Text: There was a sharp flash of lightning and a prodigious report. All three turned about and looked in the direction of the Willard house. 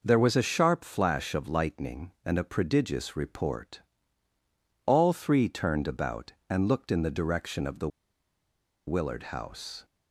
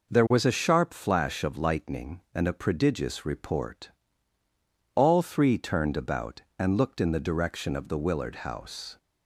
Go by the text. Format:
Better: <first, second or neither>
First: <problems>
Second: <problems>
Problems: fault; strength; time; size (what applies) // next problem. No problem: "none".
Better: second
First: pauses between "the" and "Willard"; at 7.8 s; 0.99 s long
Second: none